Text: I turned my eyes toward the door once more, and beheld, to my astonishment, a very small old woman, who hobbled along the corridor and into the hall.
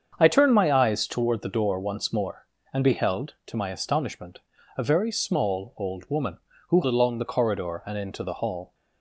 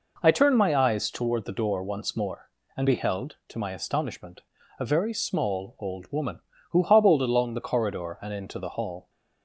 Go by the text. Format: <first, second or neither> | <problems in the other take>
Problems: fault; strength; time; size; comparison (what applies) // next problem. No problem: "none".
second | starts louder than the rest; strong; until 1.2 s; 7 dB // skips "hobbled"; at 6.8 s